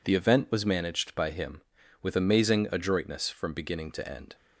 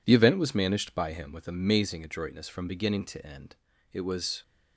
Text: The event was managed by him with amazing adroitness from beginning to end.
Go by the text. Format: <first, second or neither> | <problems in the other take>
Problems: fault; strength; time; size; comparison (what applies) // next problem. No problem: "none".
first | goes on to say "It was"; from 3.9 s on; 0.50 s long